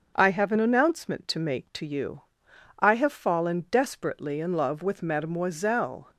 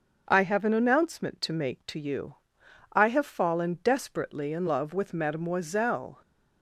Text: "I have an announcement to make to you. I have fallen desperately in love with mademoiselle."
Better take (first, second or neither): neither